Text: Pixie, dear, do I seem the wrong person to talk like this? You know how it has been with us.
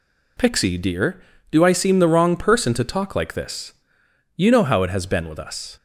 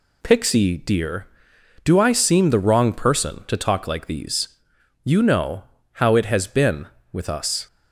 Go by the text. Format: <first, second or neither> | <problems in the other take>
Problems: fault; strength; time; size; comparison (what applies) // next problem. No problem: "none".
first | says "these" for "this"; at 4.0 s // pauses between "know" and "how"; slight; at 5.6 s; 0.30 s long